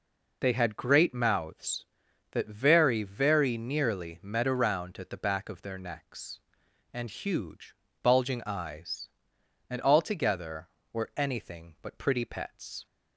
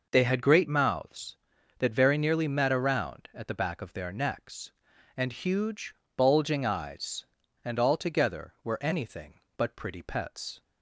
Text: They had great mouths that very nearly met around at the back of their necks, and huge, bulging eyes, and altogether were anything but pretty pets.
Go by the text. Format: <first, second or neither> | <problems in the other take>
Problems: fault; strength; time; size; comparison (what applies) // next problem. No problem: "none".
second | says "very" twice; at 3.0 s